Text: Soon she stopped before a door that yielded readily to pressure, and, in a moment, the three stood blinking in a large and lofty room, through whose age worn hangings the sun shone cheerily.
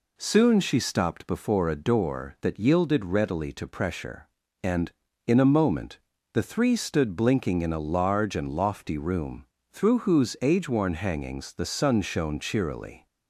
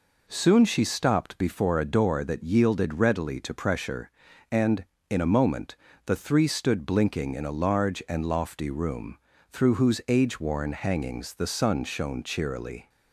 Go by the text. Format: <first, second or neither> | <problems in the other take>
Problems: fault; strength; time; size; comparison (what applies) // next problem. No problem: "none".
neither | none